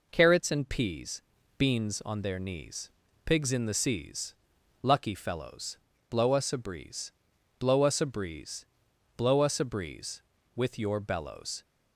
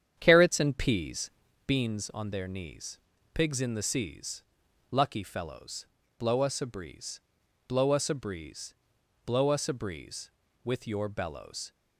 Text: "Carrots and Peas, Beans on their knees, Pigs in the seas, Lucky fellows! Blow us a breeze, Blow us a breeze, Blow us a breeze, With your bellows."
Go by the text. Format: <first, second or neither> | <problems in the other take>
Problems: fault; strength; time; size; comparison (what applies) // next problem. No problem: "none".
first | starts louder than the rest; strong; until 1.5 s; 9 dB